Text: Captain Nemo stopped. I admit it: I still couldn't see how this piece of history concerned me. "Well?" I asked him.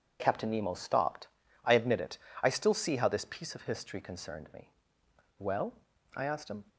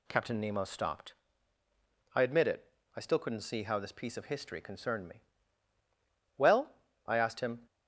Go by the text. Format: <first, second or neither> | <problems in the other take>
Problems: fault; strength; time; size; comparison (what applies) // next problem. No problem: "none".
second | skips "couldn't"; at 2.7 s